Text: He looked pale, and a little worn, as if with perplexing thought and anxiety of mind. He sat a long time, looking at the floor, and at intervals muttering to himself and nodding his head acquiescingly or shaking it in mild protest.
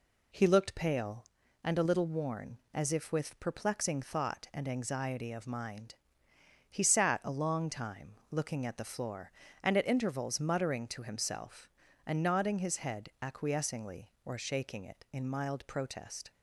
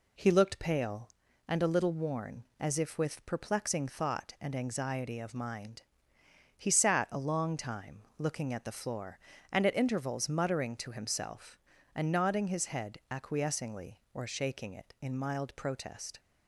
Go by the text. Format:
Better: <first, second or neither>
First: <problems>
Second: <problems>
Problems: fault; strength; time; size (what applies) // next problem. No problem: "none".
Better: neither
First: none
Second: none